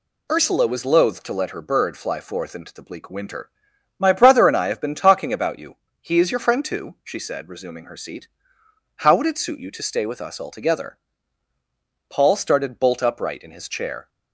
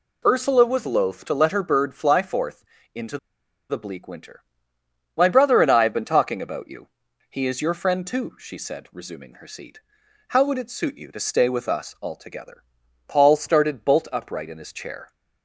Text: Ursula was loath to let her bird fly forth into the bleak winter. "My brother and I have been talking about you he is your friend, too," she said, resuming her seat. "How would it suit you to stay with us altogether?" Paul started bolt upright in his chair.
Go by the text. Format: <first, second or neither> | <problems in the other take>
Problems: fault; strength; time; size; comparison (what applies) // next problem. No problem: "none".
first | pauses between "forth" and "into"; slight; at 2.6 s; 0.30 s long // pauses between "into" and "the"; noticeable; at 3.1 s; 0.51 s long // pauses between "you" and "he"; at 6.8 s; 0.42 s long; slight in the first